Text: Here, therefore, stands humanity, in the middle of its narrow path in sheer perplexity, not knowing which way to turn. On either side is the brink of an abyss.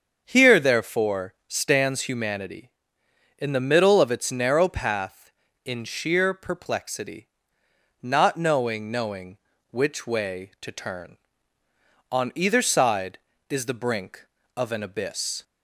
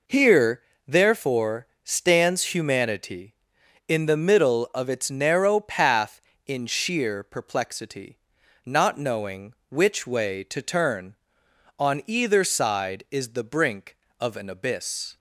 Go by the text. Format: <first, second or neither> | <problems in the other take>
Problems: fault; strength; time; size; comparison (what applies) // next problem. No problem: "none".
second | starts louder than the rest; until 1.2 s; 7 dB // says "knowing" twice; at 8.8 s